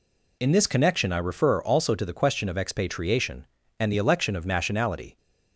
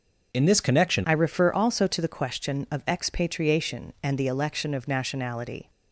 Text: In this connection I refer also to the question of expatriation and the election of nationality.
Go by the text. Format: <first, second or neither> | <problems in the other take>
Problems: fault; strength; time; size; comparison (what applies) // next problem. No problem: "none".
first | changes voice at "I"; from 1.0 s on; 4.6 s long